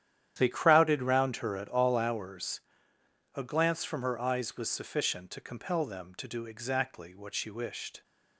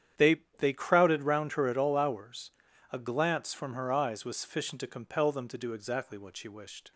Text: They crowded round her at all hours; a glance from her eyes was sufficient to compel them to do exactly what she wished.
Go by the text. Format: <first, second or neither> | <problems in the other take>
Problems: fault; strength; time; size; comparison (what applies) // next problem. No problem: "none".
first | starts louder than the rest; strong; until 1.3 s; 9.5 dB; strong in the first // says "They" twice; at 0.5 s